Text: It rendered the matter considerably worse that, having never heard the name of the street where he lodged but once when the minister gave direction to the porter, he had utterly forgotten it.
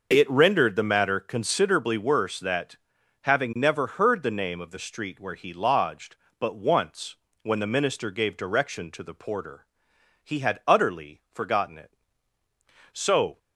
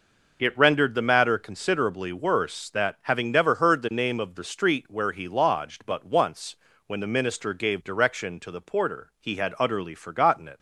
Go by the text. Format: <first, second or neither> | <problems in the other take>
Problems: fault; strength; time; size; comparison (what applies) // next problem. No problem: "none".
second | pauses between "once" and "when"; slight; at 7.1 s; 0.26 s long; slight in the second // goes on to say "So"; slight; from 12.9 s on; 0.46 s long